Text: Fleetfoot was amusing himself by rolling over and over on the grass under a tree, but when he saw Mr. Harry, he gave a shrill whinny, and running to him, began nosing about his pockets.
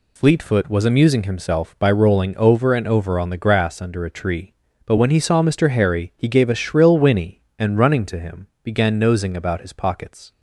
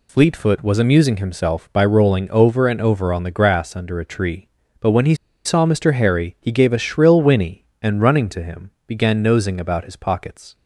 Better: first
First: none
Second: pauses between "he" and "saw"; slight; at 5.1 s; 0.30 s long

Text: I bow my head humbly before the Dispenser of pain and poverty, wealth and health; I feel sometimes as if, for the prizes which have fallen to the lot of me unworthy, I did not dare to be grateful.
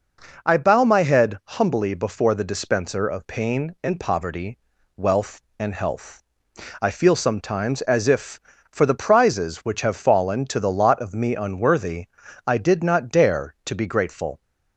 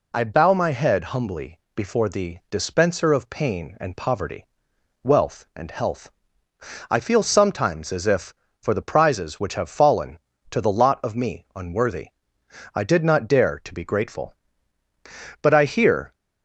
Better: first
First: none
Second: pauses between "humbly" and "before"; slight; at 1.5 s; 0.16 s long // goes on to say "But I hear"; noticeable; from 15.4 s on; 0.72 s long

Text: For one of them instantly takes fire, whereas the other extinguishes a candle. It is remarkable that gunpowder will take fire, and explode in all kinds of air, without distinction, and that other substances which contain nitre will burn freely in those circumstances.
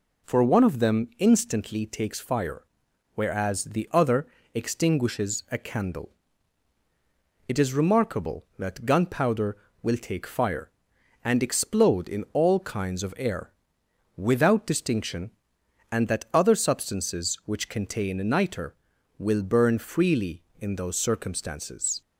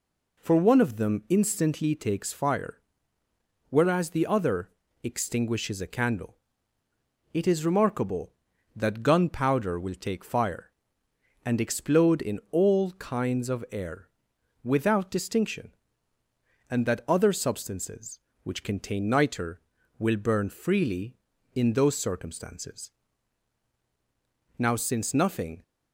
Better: first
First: pauses between "other" and "extinguishes"; slight; at 4.2 s; 0.28 s long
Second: pauses between "other" and "extinguishes"; slight; at 4.6 s; 0.34 s long // goes on to say "Now since nothing"; noticeable; from 24.5 s on; 1.0 s long

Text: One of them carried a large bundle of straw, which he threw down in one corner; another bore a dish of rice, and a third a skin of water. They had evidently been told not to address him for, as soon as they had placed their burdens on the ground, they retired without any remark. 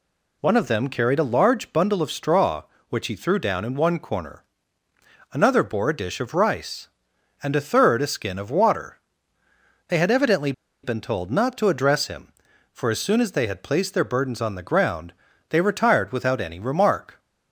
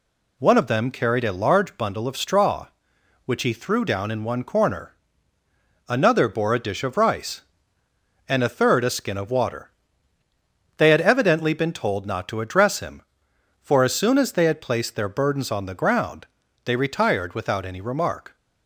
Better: second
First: pauses between "evidently" and "been"; slight; at 10.5 s; 0.31 s long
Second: none

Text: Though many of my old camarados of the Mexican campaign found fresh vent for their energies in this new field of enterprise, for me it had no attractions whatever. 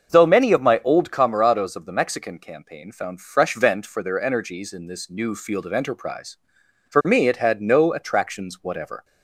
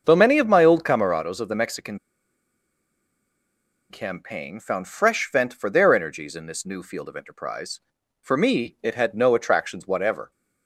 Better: first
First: starts louder than the rest; until 1.1 s; 6.5 dB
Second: starts louder than the rest; until 1.0 s; 6.5 dB // pauses between "Mexican" and "campaign"; strong; at 1.9 s; 1.9 s long

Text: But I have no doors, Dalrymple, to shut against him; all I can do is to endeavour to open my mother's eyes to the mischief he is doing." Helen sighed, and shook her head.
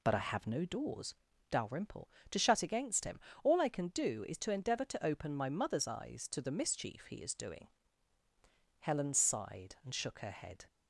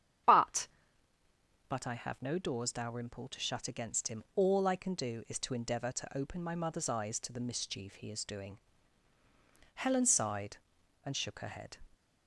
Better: first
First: none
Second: starts louder than the rest; strong; until 2.2 s; 9 dB // says "But" twice; at 1.6 s

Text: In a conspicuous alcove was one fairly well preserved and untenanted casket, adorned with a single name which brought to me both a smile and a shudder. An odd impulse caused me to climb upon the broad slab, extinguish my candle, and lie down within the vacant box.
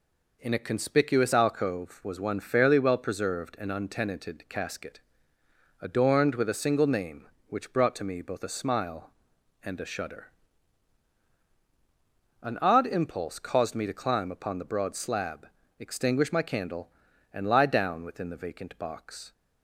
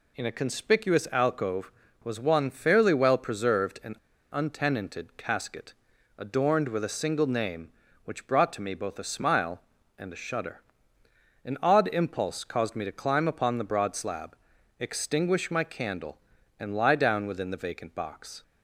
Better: first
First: none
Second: pauses between "and" and "untenanted"; at 3.9 s; 0.36 s long

